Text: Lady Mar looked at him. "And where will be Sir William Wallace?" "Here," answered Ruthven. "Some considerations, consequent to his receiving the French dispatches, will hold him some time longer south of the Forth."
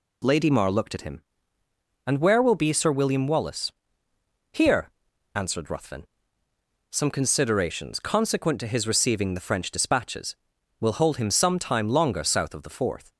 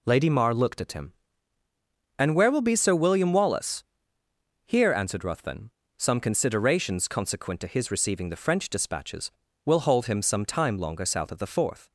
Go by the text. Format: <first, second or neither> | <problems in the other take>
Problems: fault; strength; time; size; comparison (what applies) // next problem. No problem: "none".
neither | none